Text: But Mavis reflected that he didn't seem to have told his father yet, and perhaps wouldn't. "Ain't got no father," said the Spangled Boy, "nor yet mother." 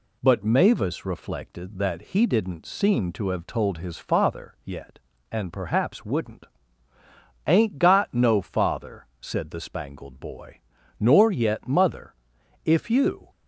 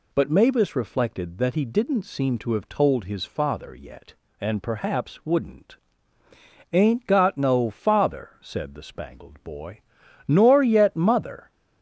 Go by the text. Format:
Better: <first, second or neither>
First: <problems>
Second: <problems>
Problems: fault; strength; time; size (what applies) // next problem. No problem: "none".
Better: second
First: goes on to say "If you"; noticeable; from 12.6 s on; 0.64 s long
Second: none